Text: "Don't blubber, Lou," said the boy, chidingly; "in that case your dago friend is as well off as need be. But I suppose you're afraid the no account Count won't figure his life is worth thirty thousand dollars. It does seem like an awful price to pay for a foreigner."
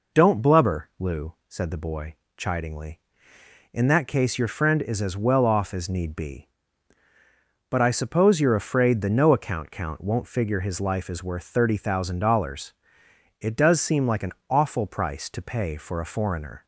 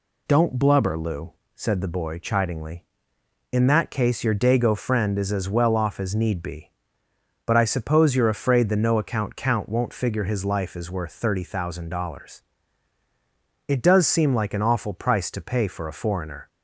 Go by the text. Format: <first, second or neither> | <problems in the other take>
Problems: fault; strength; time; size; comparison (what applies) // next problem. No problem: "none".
second | skips "dago"; at 4.4 s // pauses between "an" and "awful"; slight; at 14.3 s; 0.16 s long